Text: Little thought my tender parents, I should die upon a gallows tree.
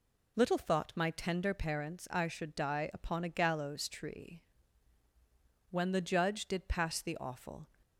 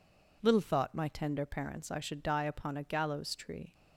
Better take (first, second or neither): second